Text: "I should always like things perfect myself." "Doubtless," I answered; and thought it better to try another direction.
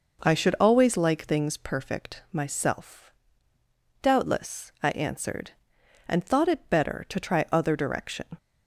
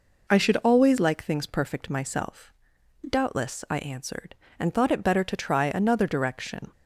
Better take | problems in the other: second | says "other" for "another"; at 7.4 s

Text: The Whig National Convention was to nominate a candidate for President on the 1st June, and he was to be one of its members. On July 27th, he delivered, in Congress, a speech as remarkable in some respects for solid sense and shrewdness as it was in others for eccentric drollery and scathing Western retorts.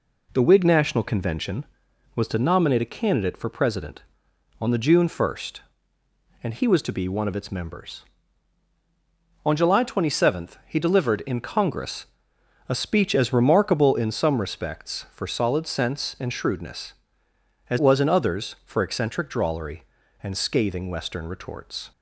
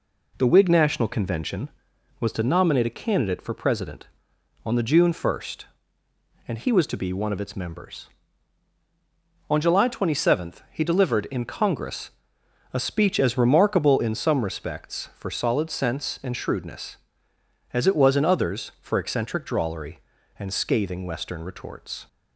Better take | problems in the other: second | skips "it"; at 17.7 s

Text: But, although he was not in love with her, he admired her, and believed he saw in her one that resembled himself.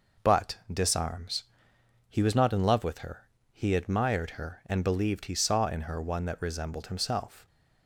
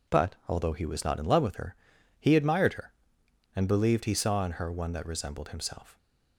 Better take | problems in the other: second | says "disarms" for "although"; at 0.7 s

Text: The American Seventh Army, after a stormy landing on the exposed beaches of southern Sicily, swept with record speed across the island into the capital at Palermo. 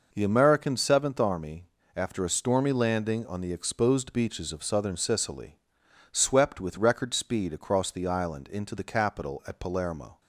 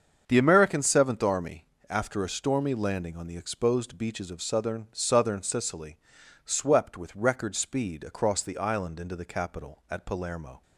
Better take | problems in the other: first | starts louder than the rest; until 1.2 s; 7 dB // says "southern" twice; at 4.9 s

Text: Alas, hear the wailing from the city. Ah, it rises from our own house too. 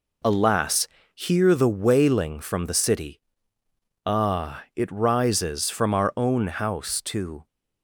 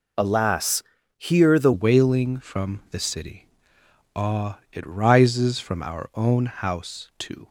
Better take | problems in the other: first | changes voice at "wailing"; from 1.7 s on; 5.7 s long

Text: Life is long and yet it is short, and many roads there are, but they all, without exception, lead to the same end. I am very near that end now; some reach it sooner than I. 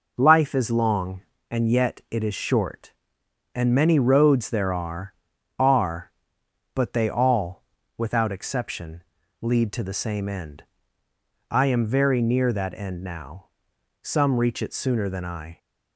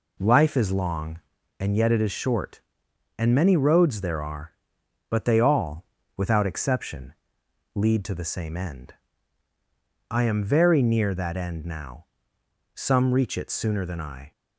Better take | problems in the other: second | says "are" twice; at 5.5 s

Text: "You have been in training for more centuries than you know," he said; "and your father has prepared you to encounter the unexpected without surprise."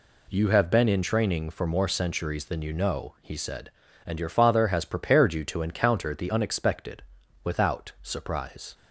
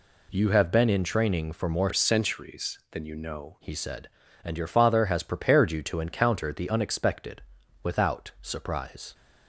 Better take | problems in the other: first | changes voice from "centuries" to "know"; from 1.9 to 3.5 s; 1.6 s long // pauses between "unexpected" and "without"; at 7.4 s; 0.42 s long; also in the first

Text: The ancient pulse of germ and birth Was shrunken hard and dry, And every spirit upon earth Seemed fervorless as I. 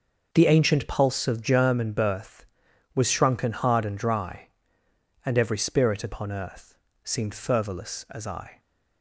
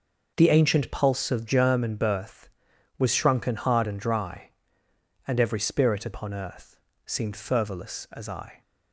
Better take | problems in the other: neither | starts louder than the rest; noticeable; the same in both // pauses between "earth" and "Seemed"; slight; the same in both

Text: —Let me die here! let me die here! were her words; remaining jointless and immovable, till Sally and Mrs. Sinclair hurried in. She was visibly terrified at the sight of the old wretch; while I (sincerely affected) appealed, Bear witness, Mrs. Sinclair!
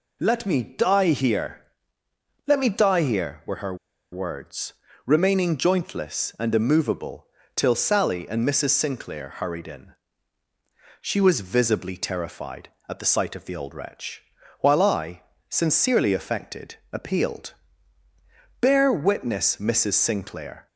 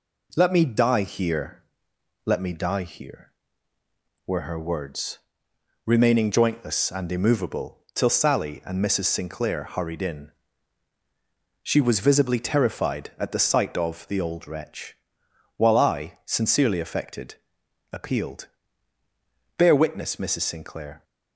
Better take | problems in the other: second | pauses between "her" and "words"; at 3.7 s; 0.37 s long

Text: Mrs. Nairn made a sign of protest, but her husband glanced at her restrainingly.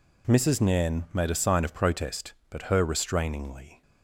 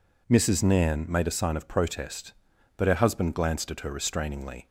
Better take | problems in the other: second | skips "husband glanced at her"; at 2.8 s

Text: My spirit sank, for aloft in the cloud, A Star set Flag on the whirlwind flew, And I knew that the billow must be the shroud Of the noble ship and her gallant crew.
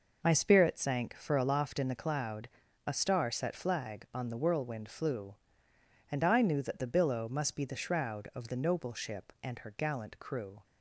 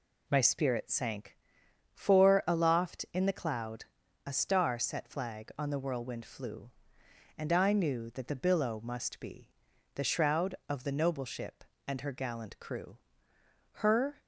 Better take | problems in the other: first | pauses between "be" and "the"; at 9.5 s; 0.42 s long // goes on to say "Her"; slight; from 13.7 s on; 0.46 s long

